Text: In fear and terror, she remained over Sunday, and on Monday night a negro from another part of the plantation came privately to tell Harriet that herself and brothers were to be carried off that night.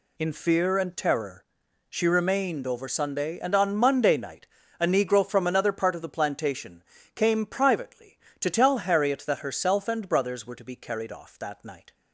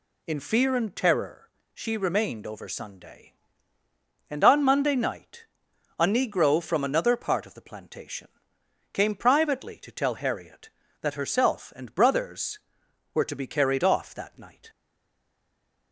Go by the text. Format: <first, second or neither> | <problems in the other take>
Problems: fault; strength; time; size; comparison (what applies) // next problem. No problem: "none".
first | pauses between "night" and "a"; noticeable; at 5.4 s; 0.53 s long; slight in the first // pauses between "plantation" and "came"; noticeable; at 8.2 s; 0.64 s long; slight in the first // stays silent after the last word; noticeable; from 14.6 s on; 1.3 s long